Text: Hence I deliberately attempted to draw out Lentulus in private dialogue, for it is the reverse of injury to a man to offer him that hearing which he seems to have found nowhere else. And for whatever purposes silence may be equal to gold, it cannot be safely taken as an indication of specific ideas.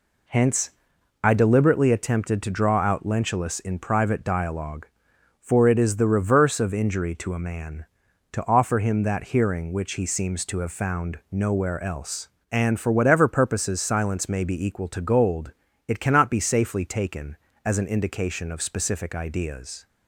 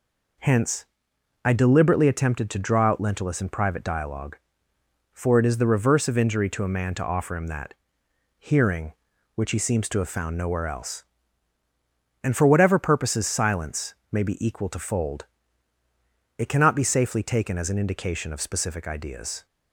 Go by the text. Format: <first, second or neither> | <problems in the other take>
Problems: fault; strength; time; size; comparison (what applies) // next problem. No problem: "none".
first | pauses between "Hence" and "I"; noticeable; at 0.8 s; 0.58 s long; noticeable in the first // pauses between "that" and "hearing"; noticeable; at 7.7 s; 0.68 s long // pauses between "silence" and "may"; slight; at 13.9 s; 0.18 s long // says "fold" for "gold"; at 14.7 s